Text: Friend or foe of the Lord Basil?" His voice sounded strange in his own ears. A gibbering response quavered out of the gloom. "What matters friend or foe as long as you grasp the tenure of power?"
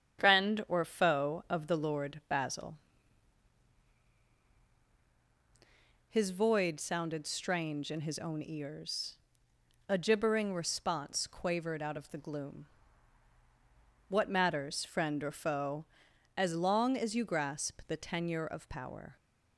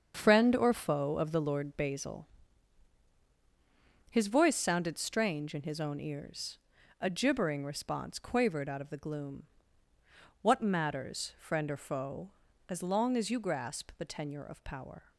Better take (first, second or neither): second